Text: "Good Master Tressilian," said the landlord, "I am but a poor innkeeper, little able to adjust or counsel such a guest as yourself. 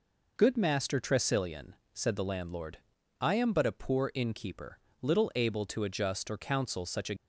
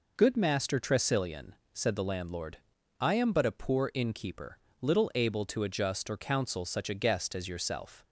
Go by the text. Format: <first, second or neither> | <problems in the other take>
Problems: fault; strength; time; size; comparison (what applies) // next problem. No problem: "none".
second | stops before "guest as yourself"; at 7.1 s